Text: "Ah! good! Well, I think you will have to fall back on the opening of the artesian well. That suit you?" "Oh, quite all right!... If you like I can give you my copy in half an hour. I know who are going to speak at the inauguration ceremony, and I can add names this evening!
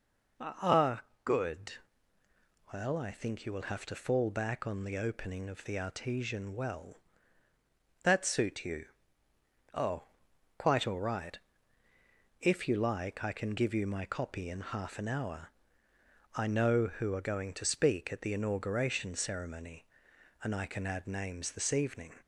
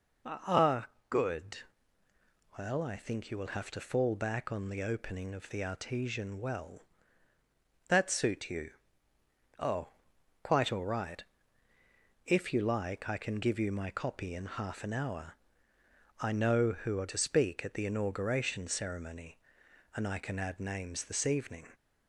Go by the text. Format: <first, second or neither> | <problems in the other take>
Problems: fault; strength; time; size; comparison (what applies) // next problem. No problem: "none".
first | skips "going"; at 17.0 s